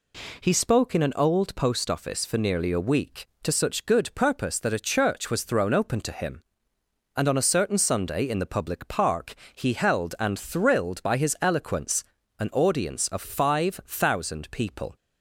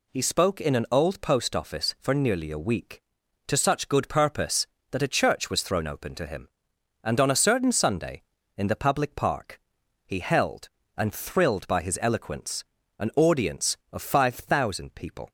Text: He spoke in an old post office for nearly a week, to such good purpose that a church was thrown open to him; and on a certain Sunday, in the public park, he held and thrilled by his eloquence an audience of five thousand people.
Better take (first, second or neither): neither